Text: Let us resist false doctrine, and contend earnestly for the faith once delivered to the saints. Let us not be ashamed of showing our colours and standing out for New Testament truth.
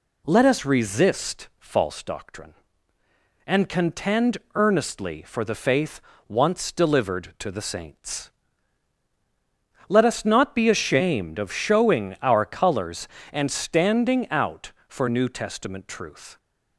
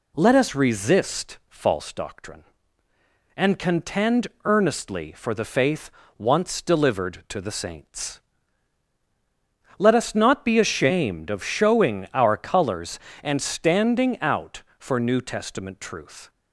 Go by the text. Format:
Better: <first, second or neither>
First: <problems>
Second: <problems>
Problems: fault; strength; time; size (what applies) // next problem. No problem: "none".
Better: neither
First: pauses between "contend" and "earnestly"; slight; at 4.3 s; 0.16 s long // pauses between "faith" and "once"; slight; at 6.0 s; 0.28 s long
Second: pauses between "contend" and "earnestly"; slight; at 4.2 s; 0.16 s long // pauses between "faith" and "once"; slight; at 5.9 s; 0.28 s long